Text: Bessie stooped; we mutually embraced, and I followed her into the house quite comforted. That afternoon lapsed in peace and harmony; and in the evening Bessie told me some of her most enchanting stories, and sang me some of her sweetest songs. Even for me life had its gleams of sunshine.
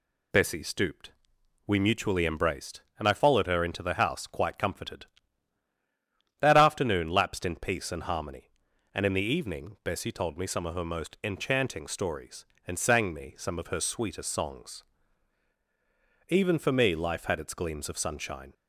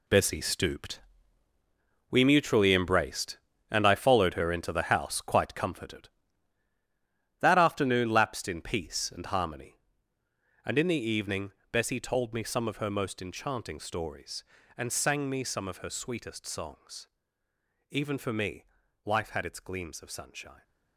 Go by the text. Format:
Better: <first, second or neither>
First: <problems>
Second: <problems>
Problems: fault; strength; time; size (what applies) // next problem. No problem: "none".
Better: first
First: none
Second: gets quieter; strong; throughout; 11 dB // pauses between "evening" and "Bessie"; slight; at 11.5 s; 0.22 s long // pauses between "me" and "life"; at 18.6 s; 0.40 s long